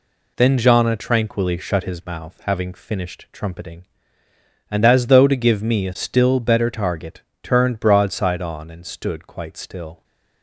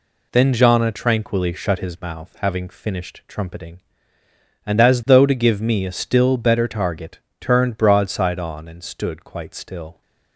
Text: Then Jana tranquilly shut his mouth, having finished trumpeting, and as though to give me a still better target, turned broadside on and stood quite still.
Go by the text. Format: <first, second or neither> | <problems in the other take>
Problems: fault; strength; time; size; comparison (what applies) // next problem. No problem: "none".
neither | none